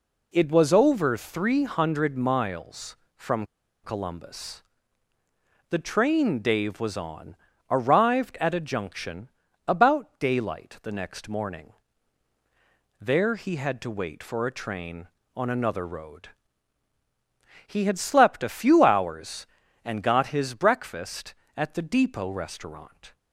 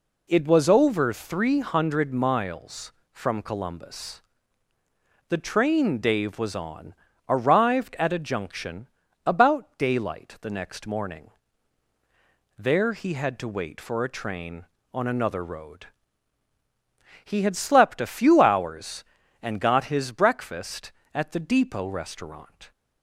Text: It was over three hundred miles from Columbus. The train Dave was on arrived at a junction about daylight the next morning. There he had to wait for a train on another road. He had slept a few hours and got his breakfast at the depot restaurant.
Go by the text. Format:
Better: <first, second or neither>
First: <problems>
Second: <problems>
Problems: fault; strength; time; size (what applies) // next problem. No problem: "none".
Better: second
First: pauses between "from" and "Columbus"; at 3.4 s; 0.39 s long // pauses between "on" and "arrived"; slight; at 7.3 s; 0.36 s long // pauses between "junction" and "about"; slight; at 9.2 s; 0.36 s long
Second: pauses between "on" and "arrived"; slight; at 6.9 s; 0.36 s long // pauses between "junction" and "about"; slight; at 8.8 s; 0.36 s long